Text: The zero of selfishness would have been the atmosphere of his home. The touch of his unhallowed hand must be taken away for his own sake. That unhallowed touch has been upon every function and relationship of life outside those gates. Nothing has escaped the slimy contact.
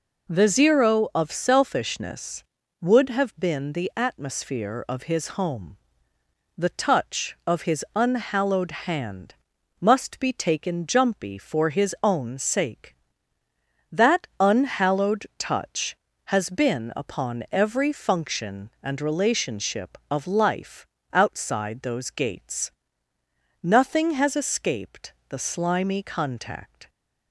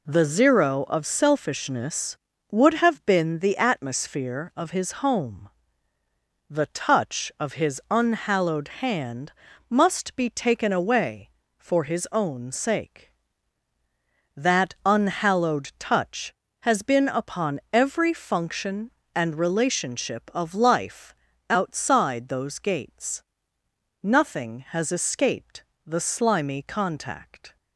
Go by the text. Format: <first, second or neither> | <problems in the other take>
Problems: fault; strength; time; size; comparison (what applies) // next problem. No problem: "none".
second | pauses between "hand" and "must"; at 9.3 s; 0.44 s long; slight in the second // says "jumpy" for "away"; at 10.8 s // pauses between "life" and "outside"; slight; at 20.8 s; 0.28 s long; slight in the second // pauses between "escaped" and "the"; slight; at 25.1 s; 0.16 s long; slight in the second